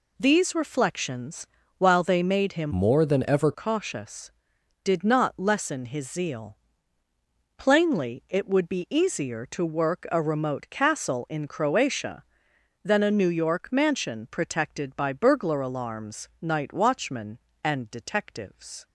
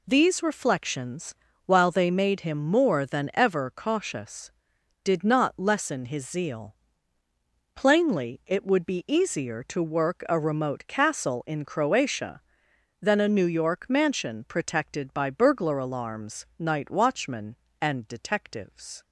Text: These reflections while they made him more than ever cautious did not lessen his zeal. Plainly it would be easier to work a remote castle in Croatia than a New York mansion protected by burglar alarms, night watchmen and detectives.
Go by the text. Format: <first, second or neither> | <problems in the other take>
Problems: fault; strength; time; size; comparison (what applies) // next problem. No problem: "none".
second | pauses between "reflections" and "while"; slight; at 1.4 s; 0.32 s long; slight in the second // changes voice from "more" to "ever"; from 2.7 to 3.5 s; 0.8 s long